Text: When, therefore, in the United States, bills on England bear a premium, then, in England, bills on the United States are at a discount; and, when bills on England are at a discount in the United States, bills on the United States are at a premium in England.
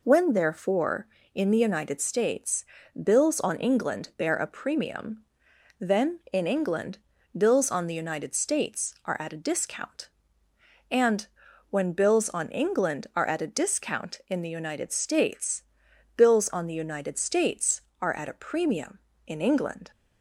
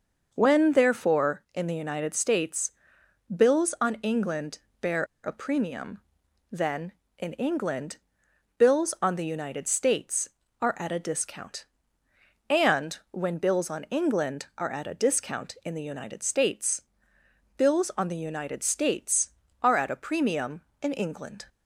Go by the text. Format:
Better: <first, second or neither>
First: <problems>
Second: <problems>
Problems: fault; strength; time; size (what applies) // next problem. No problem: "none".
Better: first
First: none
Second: pauses between "England" and "bear"; slight; at 4.5 s; 0.20 s long // pauses between "bear" and "a"; slight; at 5.0 s; 0.19 s long